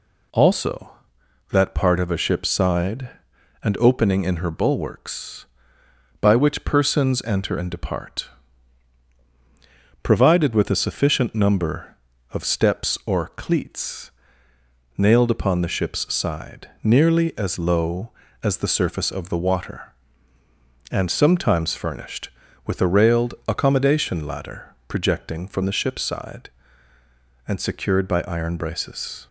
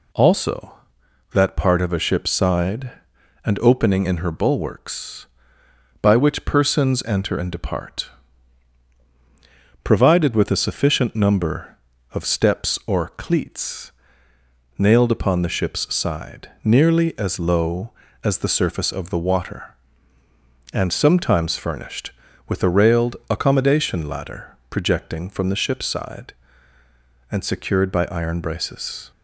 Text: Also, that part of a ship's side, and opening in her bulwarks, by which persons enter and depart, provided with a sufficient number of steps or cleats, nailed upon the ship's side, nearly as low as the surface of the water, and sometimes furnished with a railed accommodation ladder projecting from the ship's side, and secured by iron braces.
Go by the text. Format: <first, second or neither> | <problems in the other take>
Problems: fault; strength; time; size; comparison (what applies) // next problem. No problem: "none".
neither | none